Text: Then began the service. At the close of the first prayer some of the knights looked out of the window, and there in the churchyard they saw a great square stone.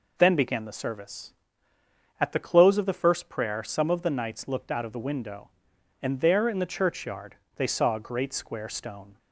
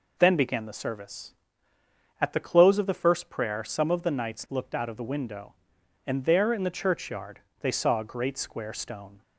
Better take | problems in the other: neither | pauses between "churchyard" and "they"; slight; the same in both

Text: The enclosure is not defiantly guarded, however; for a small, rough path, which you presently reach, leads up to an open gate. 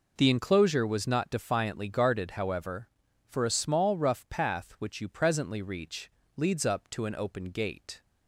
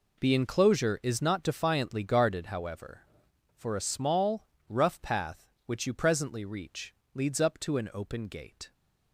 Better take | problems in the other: second | says "was" for "is"; at 0.8 s

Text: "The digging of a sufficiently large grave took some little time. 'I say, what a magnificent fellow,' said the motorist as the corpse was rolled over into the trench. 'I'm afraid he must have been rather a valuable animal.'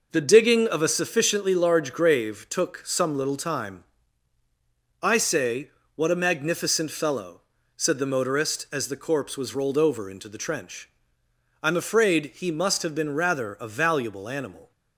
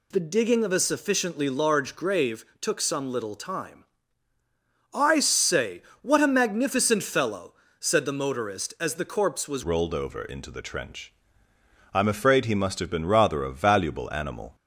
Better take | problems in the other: first | pauses between "grave" and "took"; slight; at 2.4 s; 0.16 s long // changes voice at "rolled"; from 9.6 s on; 4.9 s long

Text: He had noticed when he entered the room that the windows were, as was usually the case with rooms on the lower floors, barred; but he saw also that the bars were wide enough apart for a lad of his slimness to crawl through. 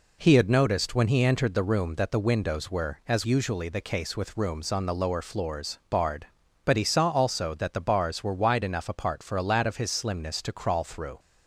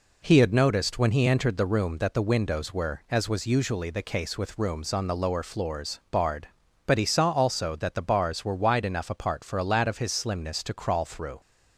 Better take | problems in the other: second | skips "was"; at 3.2 s

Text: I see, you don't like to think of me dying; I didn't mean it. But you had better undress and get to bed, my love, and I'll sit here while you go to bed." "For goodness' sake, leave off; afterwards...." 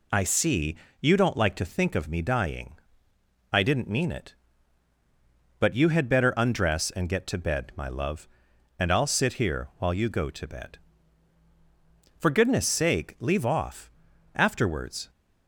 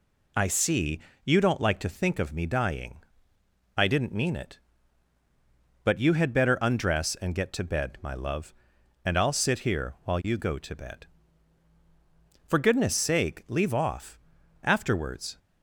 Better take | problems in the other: neither | none

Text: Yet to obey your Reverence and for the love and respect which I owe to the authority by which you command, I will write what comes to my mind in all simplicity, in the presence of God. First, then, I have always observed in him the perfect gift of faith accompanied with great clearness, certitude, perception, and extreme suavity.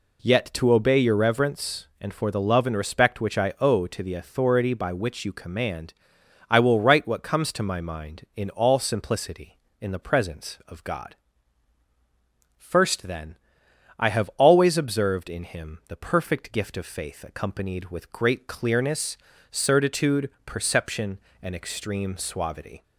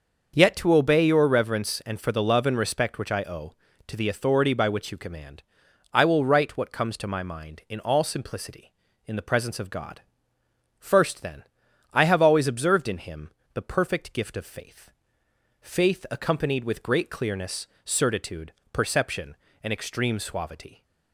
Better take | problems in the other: first | starts louder than the rest; noticeable; until 1.3 s; 6 dB // pauses between "him" and "the"; slight; at 13.3 s; 0.22 s long // says "faith" twice; at 15.6 s

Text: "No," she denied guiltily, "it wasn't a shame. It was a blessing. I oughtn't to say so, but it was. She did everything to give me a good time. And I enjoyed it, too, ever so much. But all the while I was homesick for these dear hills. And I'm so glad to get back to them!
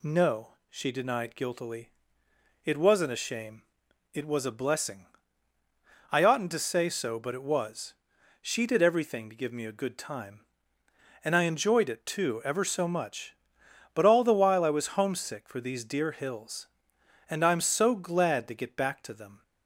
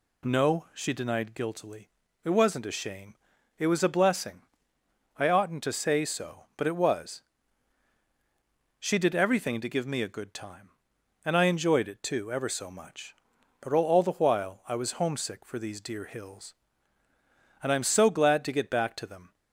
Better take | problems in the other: first | says "all" twice; at 13.8 s

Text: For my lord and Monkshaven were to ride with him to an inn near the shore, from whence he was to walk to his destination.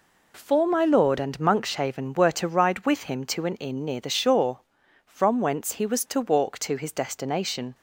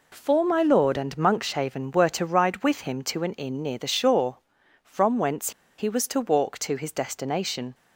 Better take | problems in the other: first | pauses between "whence" and "he"; slight; at 5.5 s; 0.27 s long

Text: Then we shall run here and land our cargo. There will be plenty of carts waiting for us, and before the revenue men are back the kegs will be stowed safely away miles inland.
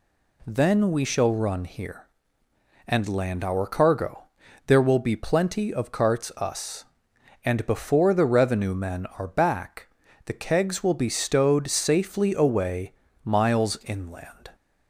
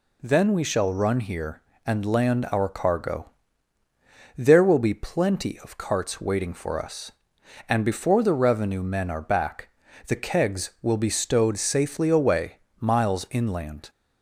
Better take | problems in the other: second | skips "waiting for"; at 6.3 s // pauses between "back" and "the"; at 9.8 s; 0.40 s long; slight in the second // pauses between "away" and "miles"; slight; at 12.9 s; 0.32 s long; slight in the second

